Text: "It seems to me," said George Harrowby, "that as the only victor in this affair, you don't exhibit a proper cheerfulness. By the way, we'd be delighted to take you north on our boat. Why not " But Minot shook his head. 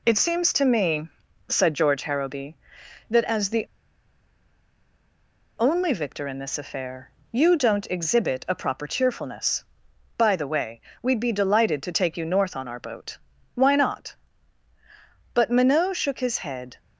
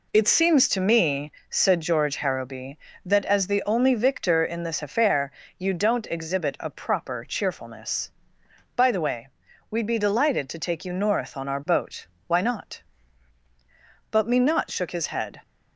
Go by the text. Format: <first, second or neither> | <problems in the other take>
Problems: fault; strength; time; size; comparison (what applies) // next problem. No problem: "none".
second | pauses between "the" and "only"; strong; at 3.6 s; 1.9 s long